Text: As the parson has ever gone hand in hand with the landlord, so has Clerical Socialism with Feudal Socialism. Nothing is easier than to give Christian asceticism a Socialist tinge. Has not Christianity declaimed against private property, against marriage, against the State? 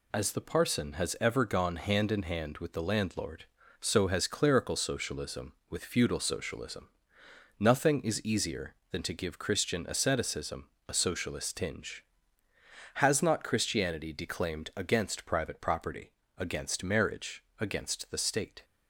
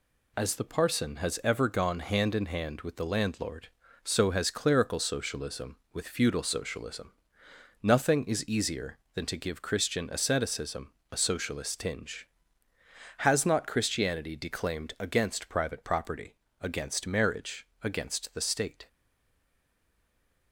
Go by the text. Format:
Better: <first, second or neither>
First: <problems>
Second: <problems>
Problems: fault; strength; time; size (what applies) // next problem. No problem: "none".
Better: first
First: pauses between "asceticism" and "a"; slight; at 10.6 s; 0.22 s long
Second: pauses between "asceticism" and "a"; slight; at 10.8 s; 0.22 s long // stays silent after the last word; noticeable; from 18.8 s on; 1.7 s long